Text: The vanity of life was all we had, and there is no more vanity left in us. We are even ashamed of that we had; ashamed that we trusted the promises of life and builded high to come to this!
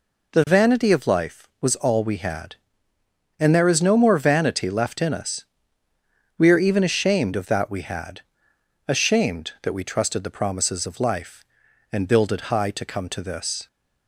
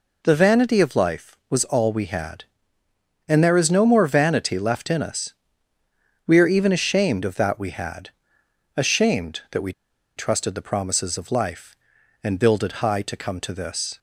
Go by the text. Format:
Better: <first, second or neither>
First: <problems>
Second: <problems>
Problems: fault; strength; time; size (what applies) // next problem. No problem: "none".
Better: first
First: none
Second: pauses between "we" and "trusted"; at 9.7 s; 0.44 s long